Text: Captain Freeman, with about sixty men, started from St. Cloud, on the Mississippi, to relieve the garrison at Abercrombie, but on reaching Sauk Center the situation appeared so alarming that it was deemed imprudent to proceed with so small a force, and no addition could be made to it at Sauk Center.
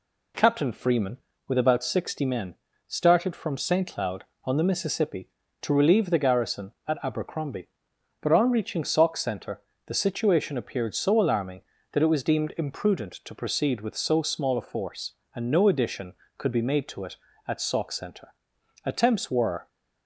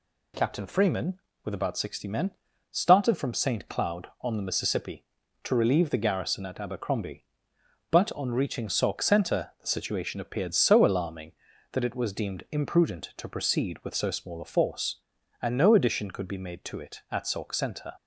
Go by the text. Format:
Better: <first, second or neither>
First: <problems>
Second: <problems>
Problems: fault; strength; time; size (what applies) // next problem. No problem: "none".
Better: second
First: pauses between "Center" and "the"; slight; at 9.6 s; 0.24 s long // goes on to say "Attempts were"; noticeable; from 18.8 s on; 0.84 s long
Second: none